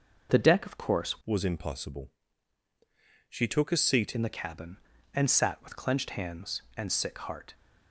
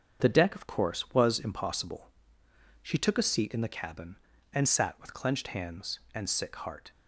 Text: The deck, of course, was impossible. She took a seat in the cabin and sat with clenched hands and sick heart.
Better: second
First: starts louder than the rest; noticeable; until 1.3 s; 6 dB // changes voice from "was" to "seat"; from 1.2 to 4.1 s; 2.9 s long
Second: starts louder than the rest; strong; until 1.2 s; 7 dB

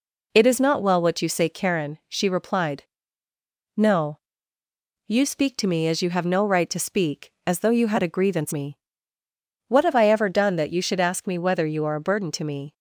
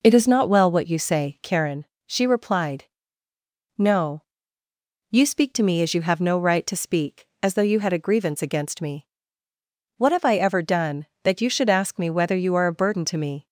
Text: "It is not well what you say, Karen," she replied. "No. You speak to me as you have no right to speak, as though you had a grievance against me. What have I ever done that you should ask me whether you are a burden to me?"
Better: second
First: skips "against"; at 8.5 s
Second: none

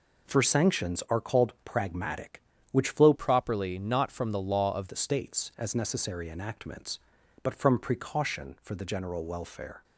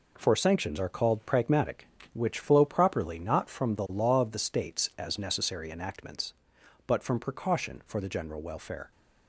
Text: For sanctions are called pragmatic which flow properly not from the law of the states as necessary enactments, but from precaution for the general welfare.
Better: second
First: changes voice from "properly" to "of"; from 3.1 to 4.8 s; 1.7 s long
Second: none

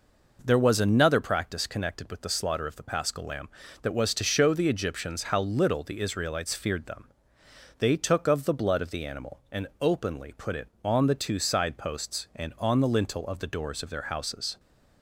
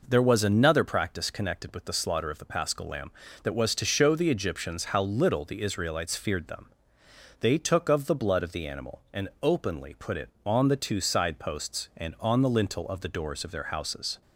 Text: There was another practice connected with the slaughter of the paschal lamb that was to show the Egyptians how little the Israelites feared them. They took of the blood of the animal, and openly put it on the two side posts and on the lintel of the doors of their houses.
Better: neither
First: none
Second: none

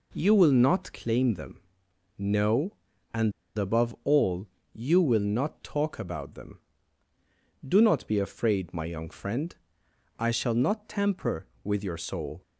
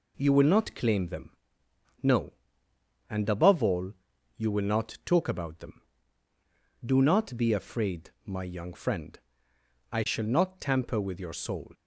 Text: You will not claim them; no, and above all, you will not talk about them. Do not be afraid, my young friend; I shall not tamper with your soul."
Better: second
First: pauses between "and" and "above"; slight; at 3.3 s; 0.25 s long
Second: none

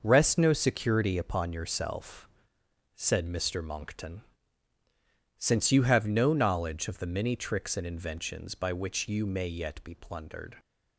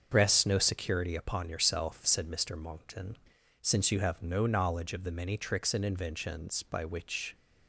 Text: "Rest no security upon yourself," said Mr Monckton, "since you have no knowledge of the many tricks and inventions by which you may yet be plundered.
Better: first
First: none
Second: starts louder than the rest; until 1.1 s; 6.5 dB // stops before "you may yet be plundered"; at 7.3 s

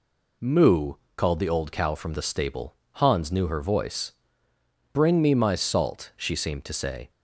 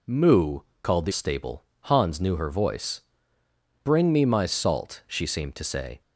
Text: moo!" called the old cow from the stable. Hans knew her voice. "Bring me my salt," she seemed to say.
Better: first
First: none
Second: skips "old cow from the"; at 1.1 s

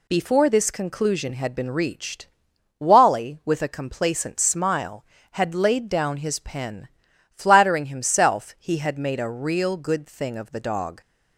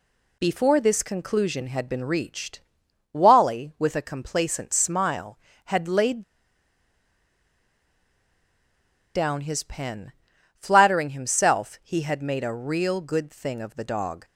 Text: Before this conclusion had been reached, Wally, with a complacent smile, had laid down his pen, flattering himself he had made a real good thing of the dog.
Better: first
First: none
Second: pauses between "laid" and "down"; strong; at 6.2 s; 2.9 s long

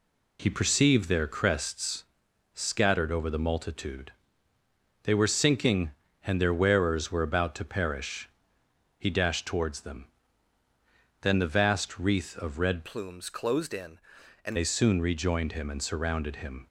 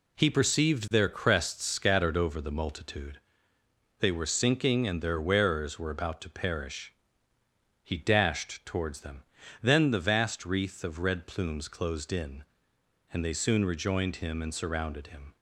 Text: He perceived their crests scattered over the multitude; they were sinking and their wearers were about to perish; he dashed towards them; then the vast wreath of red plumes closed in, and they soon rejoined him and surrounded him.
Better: second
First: pauses between "crests" and "scattered"; noticeable; at 2.0 s; 0.50 s long // changes voice from "plumes" to "and"; from 12.8 to 14.5 s; 1.7 s long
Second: none

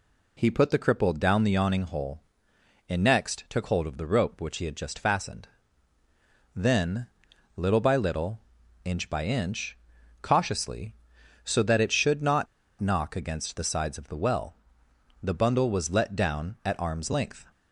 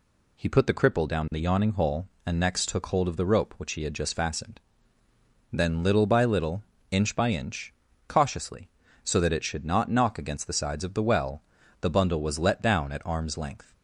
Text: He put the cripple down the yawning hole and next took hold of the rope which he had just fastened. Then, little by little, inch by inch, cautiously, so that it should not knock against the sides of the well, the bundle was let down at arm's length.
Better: second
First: pauses between "not" and "knock"; slight; at 12.4 s; 0.34 s long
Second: none

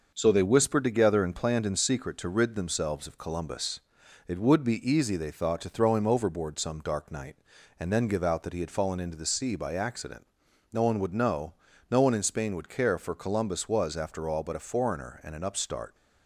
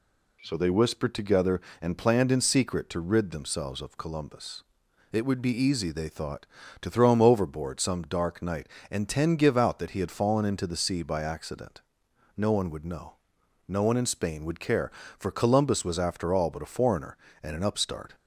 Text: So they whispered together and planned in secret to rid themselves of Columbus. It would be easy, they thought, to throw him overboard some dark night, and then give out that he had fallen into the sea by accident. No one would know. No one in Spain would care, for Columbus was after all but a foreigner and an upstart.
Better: first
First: none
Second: says "ten" for "then"; at 9.0 s

